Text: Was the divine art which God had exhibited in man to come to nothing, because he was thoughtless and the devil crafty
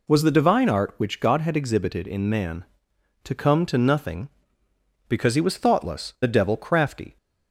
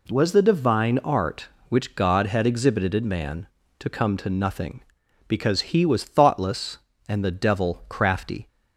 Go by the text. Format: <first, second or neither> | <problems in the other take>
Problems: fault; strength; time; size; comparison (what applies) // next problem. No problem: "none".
second | skips "and"; at 6.1 s